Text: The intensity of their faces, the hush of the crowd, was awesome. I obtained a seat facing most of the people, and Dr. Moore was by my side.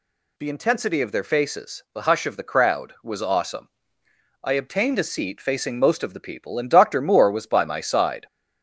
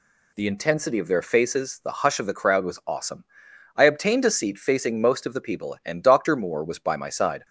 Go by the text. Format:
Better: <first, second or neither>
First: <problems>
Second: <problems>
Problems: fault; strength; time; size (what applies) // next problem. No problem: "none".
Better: second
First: gets louder; slight; throughout; 2.5 dB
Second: none